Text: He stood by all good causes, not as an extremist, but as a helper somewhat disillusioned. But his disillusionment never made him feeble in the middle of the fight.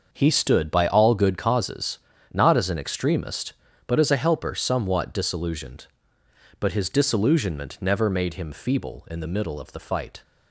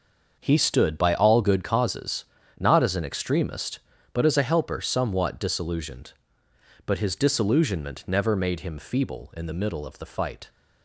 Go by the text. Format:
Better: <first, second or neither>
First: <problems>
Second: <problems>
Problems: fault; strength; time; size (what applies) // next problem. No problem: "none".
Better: neither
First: starts louder than the rest; until 1.1 s; 6.5 dB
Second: starts louder than the rest; until 1.3 s; 6.5 dB